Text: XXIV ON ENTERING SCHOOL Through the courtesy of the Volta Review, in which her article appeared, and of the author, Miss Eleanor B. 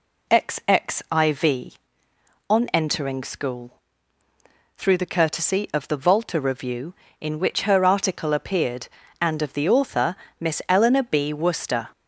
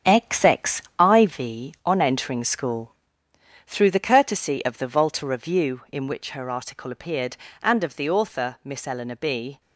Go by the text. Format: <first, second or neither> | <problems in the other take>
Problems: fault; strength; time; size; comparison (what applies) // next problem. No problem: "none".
second | pauses between "SCHOOL" and "Through"; at 3.7 s; 1.0 s long; noticeable in the second // goes on to say "Worcester"; from 11.3 s on; 0.56 s long